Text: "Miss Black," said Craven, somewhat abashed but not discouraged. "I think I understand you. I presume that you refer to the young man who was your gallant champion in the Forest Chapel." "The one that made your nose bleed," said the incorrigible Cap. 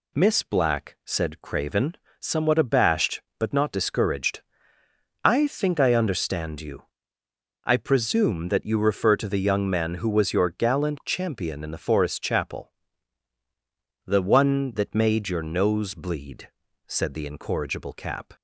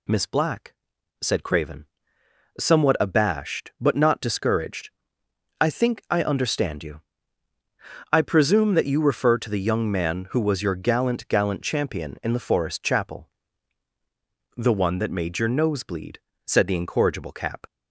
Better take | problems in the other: first | says "gallant" twice; at 11.2 s

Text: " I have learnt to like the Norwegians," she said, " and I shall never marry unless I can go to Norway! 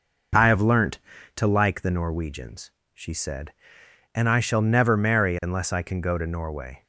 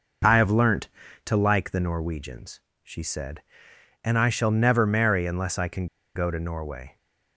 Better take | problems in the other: first | pauses between "can" and "go"; slight; at 5.8 s; 0.30 s long

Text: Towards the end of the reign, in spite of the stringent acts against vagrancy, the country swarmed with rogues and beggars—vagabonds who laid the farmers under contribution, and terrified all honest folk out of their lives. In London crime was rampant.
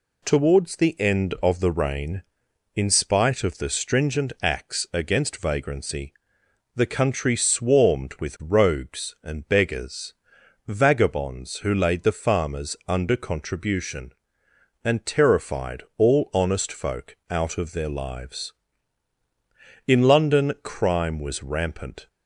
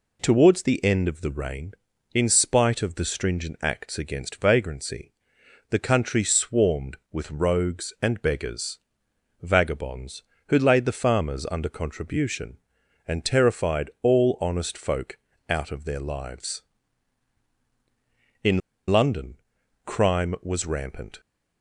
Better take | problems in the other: first | pauses between "folk" and "out"; slight; at 15.1 s; 0.32 s long // pauses between "In" and "London"; slight; at 18.6 s; 0.31 s long // pauses between "London" and "crime"; noticeable; at 19.3 s; 0.50 s long

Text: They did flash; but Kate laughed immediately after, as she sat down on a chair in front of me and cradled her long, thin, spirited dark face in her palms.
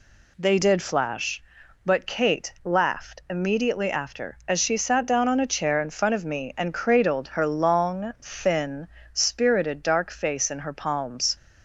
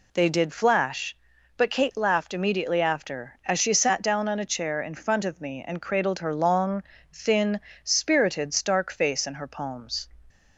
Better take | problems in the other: first | says "stark" for "dark"; at 8.5 s

